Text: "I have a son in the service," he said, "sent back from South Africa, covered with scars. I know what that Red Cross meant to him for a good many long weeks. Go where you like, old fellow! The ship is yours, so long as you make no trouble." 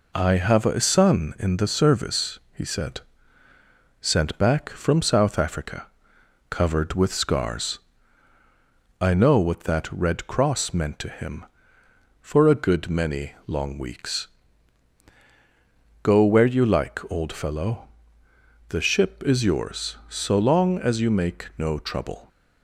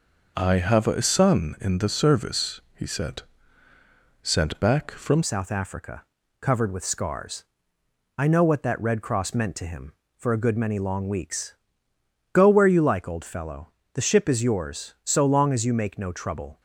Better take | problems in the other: first | changes voice at "South"; from 5.2 s on; 11.4 s long

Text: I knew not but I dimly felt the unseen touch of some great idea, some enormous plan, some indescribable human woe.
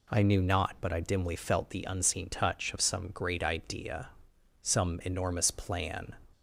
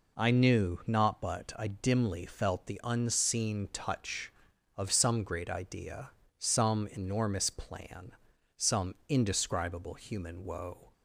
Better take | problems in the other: second | stops before "some indescribable human woe"; at 6.3 s

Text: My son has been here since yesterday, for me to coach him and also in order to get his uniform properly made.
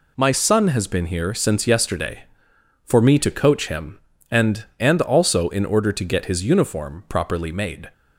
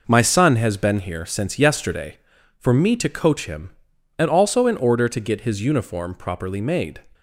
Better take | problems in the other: second | says "and" twice; at 4.7 s

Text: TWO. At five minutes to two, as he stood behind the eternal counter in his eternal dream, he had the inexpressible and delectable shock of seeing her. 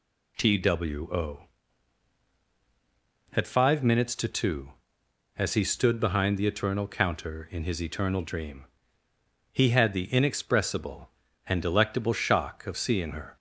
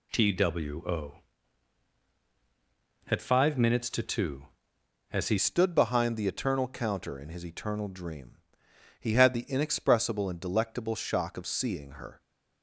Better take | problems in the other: first | changes voice at "stood"; from 5.3 s on; 6.9 s long

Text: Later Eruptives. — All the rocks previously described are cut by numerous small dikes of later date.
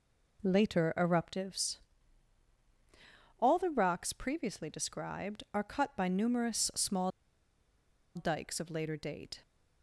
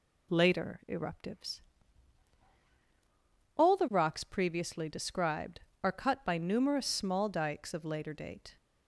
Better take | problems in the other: second | pauses between "small" and "dikes"; at 7.1 s; 1.0 s long

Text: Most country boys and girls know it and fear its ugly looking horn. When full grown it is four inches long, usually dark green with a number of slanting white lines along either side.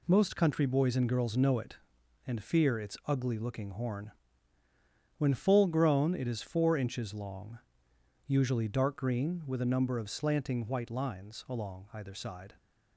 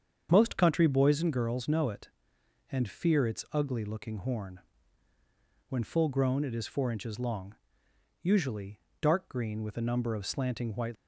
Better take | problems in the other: first | starts louder than the rest; strong; until 1.3 s; 7.5 dB // pauses between "usually" and "dark"; slight; at 8.7 s; 0.22 s long // stops before "lines along either side"; at 10.9 s

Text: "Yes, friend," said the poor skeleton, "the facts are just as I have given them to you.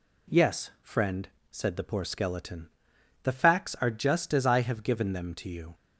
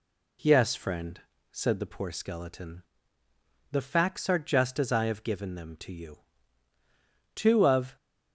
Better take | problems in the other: first | goes on to say "Two of"; noticeable; from 7.3 s on; 0.62 s long

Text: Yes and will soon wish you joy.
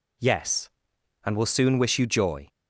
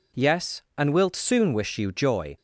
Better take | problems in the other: first | says "wilt" for "will"; at 0.9 s

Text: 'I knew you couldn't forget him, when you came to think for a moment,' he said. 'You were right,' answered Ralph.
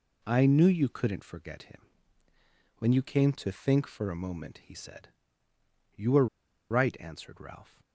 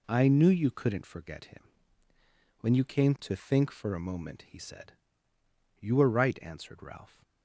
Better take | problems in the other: second | pauses between "were" and "right"; at 6.2 s; 0.44 s long

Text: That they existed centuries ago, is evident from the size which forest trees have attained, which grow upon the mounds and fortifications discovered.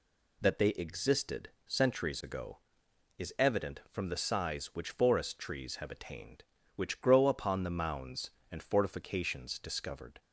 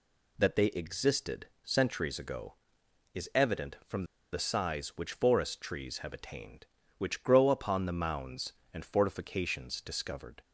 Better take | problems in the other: first | pauses between "existed" and "centuries"; slight; at 1.4 s; 0.18 s long; slight in the first // pauses between "from" and "the"; slight; at 4.0 s; 0.27 s long

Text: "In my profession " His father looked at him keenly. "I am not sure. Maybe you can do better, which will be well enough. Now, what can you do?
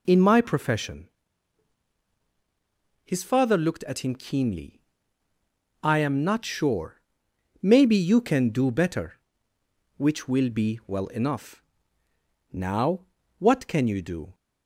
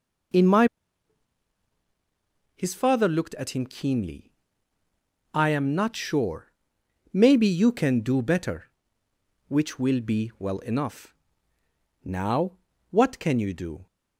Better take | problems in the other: first | skips "profession"; at 1.1 s

